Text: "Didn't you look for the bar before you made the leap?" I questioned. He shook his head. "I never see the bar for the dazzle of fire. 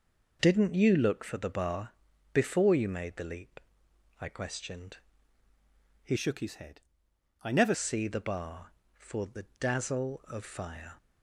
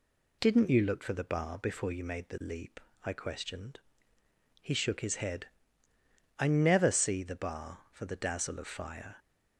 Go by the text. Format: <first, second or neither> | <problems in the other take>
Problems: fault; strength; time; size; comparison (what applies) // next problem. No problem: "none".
second | pauses between "bar" and "before"; at 1.9 s; 0.40 s long // changes voice from "shook" to "never"; from 6.1 to 7.7 s; 1.6 s long // pauses between "the" and "dazzle"; slight; at 9.4 s; 0.16 s long